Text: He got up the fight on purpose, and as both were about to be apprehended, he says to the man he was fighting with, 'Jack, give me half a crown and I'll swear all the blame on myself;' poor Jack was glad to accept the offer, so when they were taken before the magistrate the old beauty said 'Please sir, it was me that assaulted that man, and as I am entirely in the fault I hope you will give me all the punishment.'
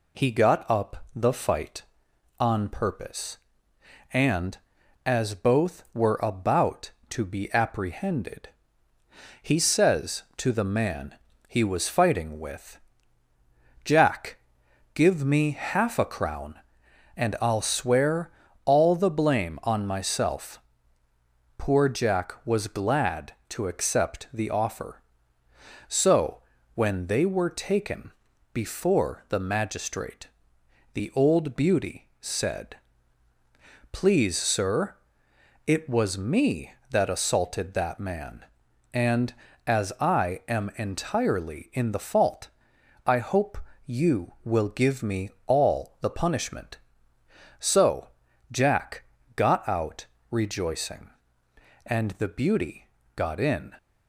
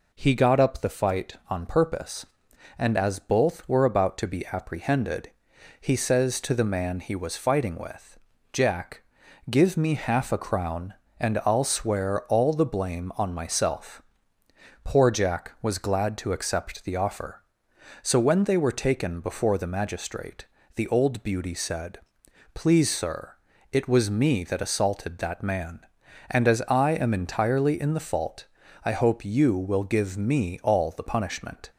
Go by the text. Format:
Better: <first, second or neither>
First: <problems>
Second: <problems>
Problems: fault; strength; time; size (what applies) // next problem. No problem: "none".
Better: second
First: pauses between "man" and "he"; slight; at 11.1 s; 0.32 s long // pauses between "swear" and "all"; slight; at 18.2 s; 0.34 s long // pauses between "so" and "when"; slight; at 26.4 s; 0.32 s long // pauses between "taken" and "before"; at 28.1 s; 0.40 s long // pauses between "magistrate" and "the"; noticeable; at 30.2 s; 0.66 s long // pauses between "said" and "Please"; at 32.7 s; 1.1 s long // pauses between "fault" and "I"; noticeable; at 42.4 s; 0.58 s long // pauses between "hope" and "you"; slight; at 43.5 s; 0.26 s long // pauses between "me" and "all"; slight; at 45.2 s; 0.16 s long // goes on to say "So Jack got out rejoicing and the beauty got in"; strong; from 47.5 s on; 6.1 s long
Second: pauses between "magistrate" and "the"; slight; at 20.4 s; 0.28 s long // pauses between "said" and "Please"; noticeable; at 22.0 s; 0.54 s long // pauses between "fault" and "I"; at 28.4 s; 0.38 s long